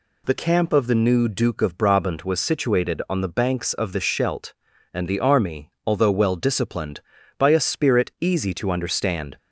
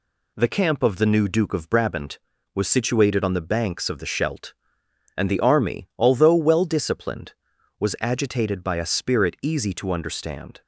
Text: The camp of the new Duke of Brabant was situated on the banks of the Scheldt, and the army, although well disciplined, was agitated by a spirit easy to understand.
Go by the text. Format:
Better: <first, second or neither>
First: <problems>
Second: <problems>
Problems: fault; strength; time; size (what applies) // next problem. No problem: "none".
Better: second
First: skips "was agitated"; at 7.1 s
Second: none